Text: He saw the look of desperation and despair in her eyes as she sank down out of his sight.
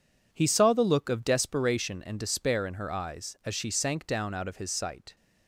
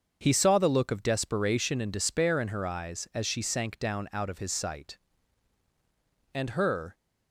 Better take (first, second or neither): first